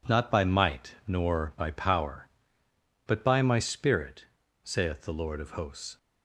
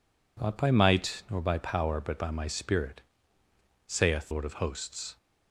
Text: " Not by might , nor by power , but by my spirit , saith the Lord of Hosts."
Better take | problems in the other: first | skips "the"; at 4.3 s

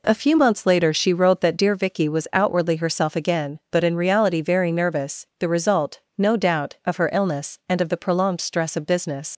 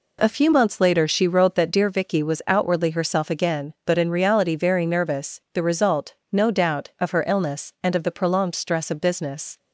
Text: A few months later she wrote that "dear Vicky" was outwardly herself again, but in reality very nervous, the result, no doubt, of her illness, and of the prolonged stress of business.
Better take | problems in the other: second | leaves "business" unfinished; at 9.3 s; 80 ms

